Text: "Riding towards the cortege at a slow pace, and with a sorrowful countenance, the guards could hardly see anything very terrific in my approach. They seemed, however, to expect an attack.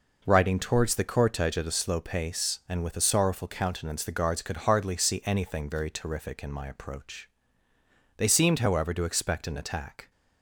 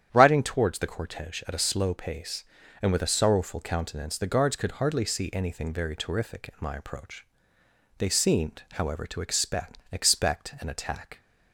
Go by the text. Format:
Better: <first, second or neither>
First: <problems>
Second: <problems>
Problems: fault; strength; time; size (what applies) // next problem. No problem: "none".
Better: first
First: none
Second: starts louder than the rest; strong; until 1.1 s; 9.5 dB // says "expect" twice; at 9.9 s